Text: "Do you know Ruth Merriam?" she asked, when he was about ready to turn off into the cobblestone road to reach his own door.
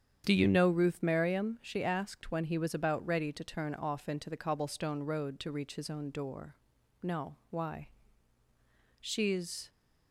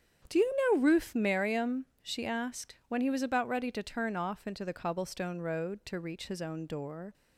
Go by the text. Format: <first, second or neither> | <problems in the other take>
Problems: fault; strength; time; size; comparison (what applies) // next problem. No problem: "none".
second | starts louder than the rest; strong; until 1.2 s; 8.5 dB; strong in the second // goes on to say "No why She's"; strong; from 7.0 s on; 2.6 s long